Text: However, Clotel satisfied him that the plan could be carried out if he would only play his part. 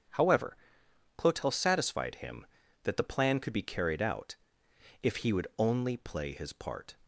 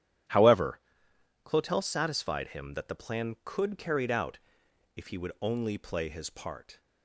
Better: first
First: starts louder than the rest; strong; until 1.7 s; 8.5 dB // pauses between "out" and "if"; noticeable; at 4.3 s; 0.68 s long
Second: starts louder than the rest; strong; until 1.9 s; 11 dB // skips "be"; at 3.7 s // pauses between "out" and "if"; noticeable; at 4.3 s; 0.58 s long

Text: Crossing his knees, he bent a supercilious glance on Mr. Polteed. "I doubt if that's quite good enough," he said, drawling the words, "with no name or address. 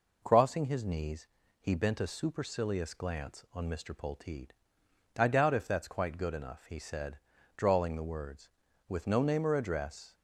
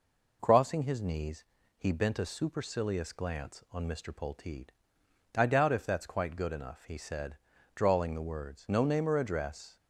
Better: first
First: none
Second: skips "with"; at 8.6 s

